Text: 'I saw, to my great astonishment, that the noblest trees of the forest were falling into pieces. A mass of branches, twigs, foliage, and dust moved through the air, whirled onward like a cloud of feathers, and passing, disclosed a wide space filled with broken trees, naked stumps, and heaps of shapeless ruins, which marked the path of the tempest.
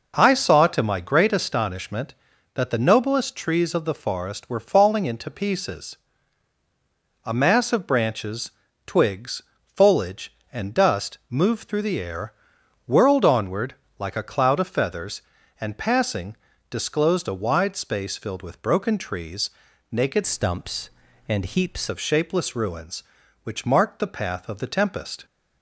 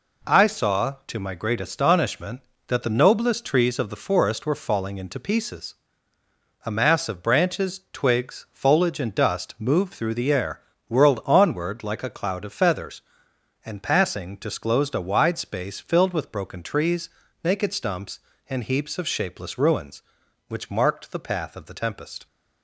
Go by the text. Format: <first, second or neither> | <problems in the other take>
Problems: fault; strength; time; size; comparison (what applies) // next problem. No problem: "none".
second | pauses between "onward" and "like"; slight; at 13.7 s; 0.24 s long // changes voice from "stumps" to "heaps"; from 20.2 to 21.8 s; 1.6 s long